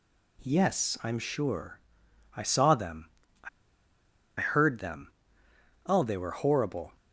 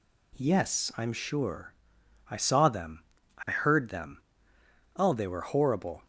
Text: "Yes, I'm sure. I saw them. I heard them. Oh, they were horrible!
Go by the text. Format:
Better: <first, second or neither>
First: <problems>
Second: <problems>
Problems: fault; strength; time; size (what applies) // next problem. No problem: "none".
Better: second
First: pauses between "I" and "heard"; noticeable; at 3.4 s; 0.90 s long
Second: none